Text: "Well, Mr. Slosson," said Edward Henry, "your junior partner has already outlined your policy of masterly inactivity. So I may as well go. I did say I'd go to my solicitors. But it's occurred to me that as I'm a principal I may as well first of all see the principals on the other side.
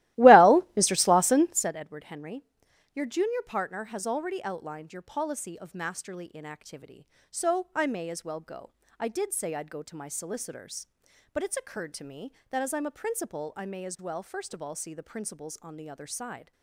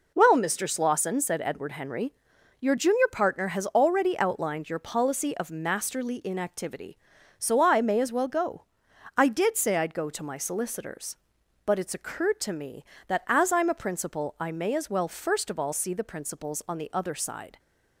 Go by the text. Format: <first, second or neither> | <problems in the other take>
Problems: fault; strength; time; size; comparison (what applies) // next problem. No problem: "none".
second | starts louder than the rest; strong; until 1.7 s; 17 dB